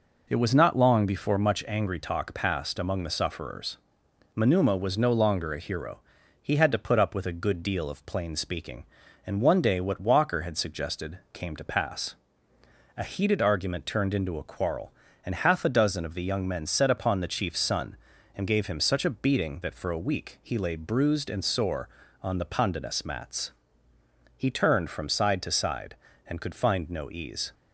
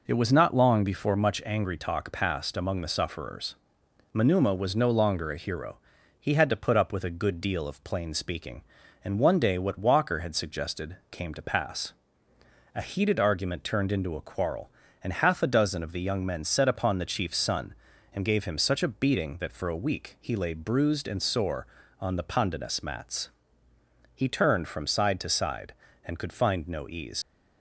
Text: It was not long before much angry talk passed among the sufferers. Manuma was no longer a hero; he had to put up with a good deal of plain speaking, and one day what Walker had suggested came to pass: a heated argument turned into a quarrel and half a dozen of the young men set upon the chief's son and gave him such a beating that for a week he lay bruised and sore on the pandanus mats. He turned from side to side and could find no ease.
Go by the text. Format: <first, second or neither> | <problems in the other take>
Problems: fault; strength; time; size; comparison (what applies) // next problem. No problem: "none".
first | leaves "ease" unfinished; at 27.2 s; 95 ms